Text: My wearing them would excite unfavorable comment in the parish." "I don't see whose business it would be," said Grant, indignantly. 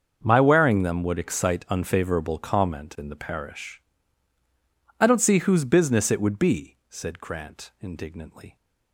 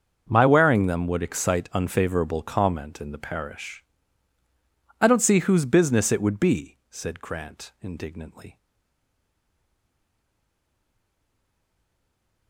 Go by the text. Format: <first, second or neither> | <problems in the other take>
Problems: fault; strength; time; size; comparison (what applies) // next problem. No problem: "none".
first | starts louder than the rest; until 1.3 s; 6.5 dB; also in the first // stays silent after the last word; strong; from 8.5 s on; 3.9 s long